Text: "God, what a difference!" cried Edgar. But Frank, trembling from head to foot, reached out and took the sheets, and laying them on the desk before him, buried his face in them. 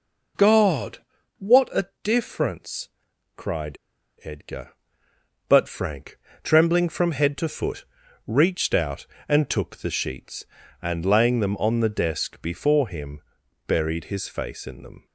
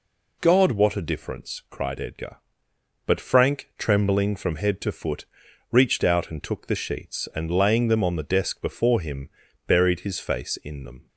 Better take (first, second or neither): second